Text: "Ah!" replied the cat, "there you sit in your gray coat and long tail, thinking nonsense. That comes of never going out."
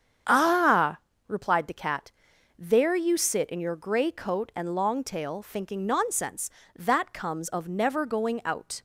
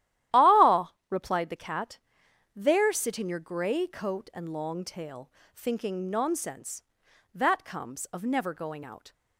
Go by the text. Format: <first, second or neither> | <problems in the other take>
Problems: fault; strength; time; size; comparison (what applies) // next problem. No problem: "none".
first | starts louder than the rest; strong; until 1.5 s; 13 dB; strong in the first // skips "you"; at 2.9 s